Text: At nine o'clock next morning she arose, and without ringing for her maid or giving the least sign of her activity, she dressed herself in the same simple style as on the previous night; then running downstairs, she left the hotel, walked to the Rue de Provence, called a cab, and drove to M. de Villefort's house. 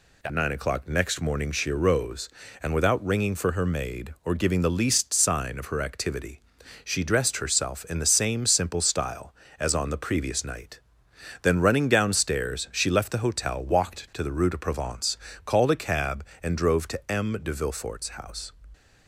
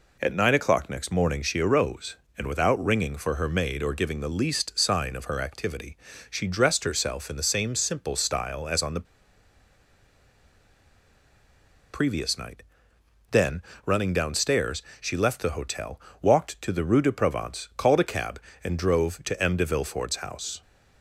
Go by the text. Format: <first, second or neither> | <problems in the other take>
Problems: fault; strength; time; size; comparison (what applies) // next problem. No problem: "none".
first | pauses between "the" and "previous"; strong; at 9.0 s; 2.8 s long // pauses between "then" and "running"; slight; at 13.6 s; 0.24 s long